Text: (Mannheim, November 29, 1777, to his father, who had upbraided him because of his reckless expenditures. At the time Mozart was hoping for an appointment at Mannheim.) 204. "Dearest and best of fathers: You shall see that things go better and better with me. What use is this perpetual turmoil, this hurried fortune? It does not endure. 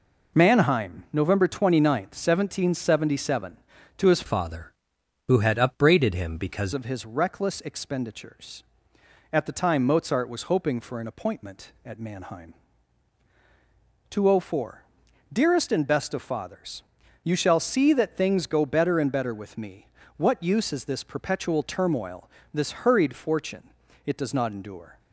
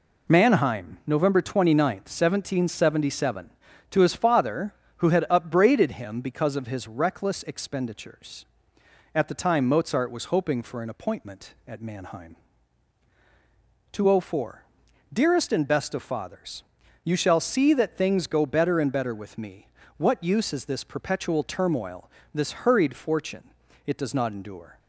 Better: second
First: changes voice from "father" to "because"; from 4.2 to 6.7 s; 2.5 s long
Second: none

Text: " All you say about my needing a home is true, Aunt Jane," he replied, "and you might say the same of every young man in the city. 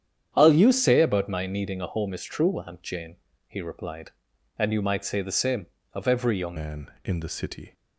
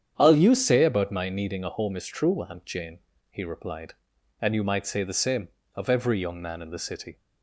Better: second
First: starts louder than the rest; strong; until 1.3 s; 9 dB // changes voice at "man"; from 6.5 s on; 1.2 s long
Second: starts louder than the rest; strong; until 1.1 s; 8.5 dB

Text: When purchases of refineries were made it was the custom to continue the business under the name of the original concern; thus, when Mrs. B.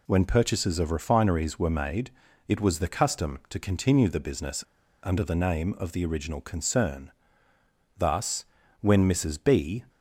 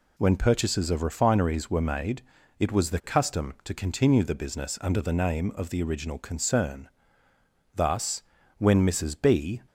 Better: second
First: pauses between "made" and "it"; slight; at 2.1 s; 0.36 s long // pauses between "business" and "under"; at 4.6 s; 0.41 s long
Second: pauses between "made" and "it"; slight; at 2.2 s; 0.36 s long

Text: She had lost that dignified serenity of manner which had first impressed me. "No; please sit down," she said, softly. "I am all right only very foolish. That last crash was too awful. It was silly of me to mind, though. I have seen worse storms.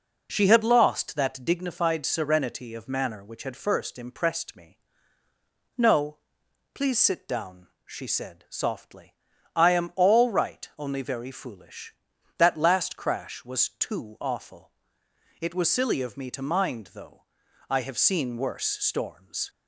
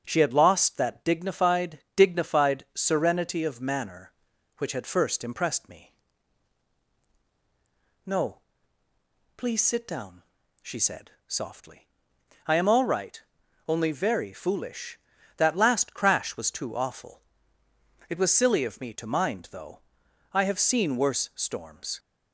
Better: first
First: none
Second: starts louder than the rest; until 1.0 s; 6.5 dB // says "dignified" twice; at 1.9 s // pauses between "right" and "only"; noticeable; at 13.1 s; 0.48 s long

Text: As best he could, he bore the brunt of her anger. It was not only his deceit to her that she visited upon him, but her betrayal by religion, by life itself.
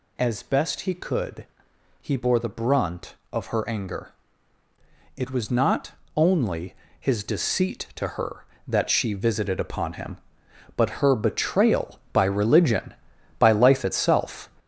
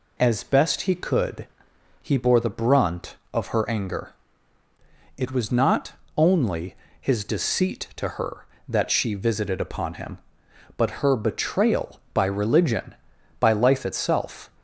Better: second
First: gets louder; throughout; 6.5 dB // pauses between "not" and "only"; slight; at 5.9 s; 0.26 s long // pauses between "only" and "his"; slight; at 6.7 s; 0.24 s long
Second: pauses between "not" and "only"; slight; at 5.9 s; 0.26 s long // pauses between "only" and "his"; slight; at 6.7 s; 0.24 s long

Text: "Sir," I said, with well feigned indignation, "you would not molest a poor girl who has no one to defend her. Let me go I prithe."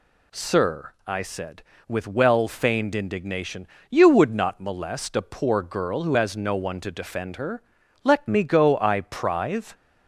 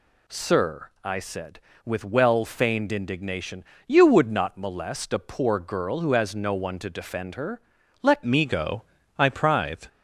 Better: first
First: none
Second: changes voice at "me"; from 8.2 s on; 1.6 s long // pauses between "go" and "I"; slight; at 8.8 s; 0.36 s long

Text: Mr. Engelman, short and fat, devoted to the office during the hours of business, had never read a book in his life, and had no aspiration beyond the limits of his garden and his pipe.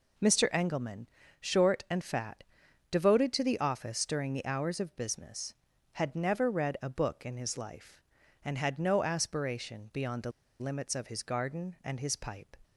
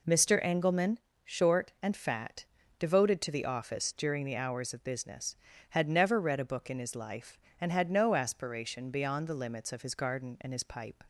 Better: second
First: pauses between "the" and "limits"; slight; at 10.3 s; 0.29 s long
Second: none

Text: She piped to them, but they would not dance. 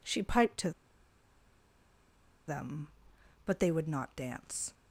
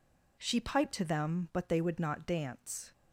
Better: second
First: pauses between "to" and "them"; strong; at 0.7 s; 1.7 s long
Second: none

